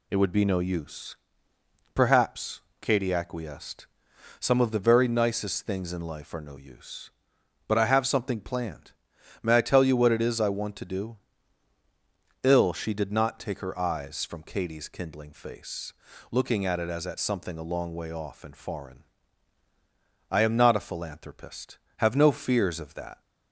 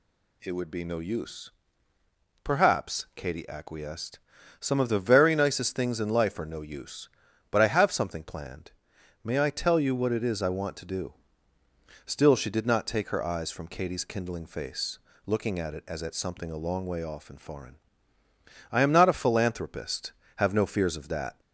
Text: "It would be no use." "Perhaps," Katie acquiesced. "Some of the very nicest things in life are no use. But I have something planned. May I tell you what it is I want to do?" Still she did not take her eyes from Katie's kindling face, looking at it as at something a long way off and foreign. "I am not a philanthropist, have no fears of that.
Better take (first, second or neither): second